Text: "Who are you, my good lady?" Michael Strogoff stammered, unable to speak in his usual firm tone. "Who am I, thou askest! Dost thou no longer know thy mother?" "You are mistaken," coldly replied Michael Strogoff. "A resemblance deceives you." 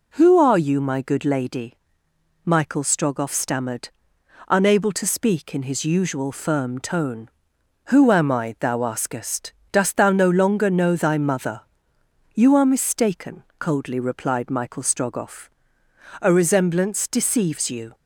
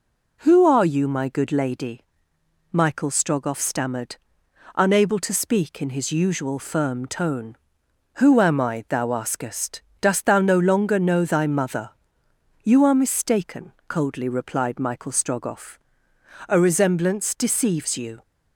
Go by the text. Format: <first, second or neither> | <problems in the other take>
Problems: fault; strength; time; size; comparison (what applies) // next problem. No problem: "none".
neither | none